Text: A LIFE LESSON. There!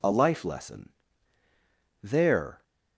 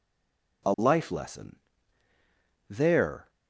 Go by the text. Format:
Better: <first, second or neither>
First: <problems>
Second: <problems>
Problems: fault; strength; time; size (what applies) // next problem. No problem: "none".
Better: first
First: none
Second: stays silent before the first word; slight; until 0.6 s; 0.6 s long